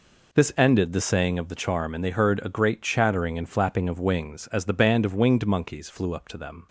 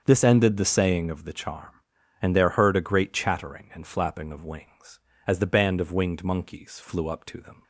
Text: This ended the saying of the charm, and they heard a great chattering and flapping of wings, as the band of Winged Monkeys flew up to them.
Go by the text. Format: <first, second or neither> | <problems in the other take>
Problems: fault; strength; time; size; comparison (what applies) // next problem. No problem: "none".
first | starts louder than the rest; until 1.0 s; 7 dB // says "there" for "they"; at 2.3 s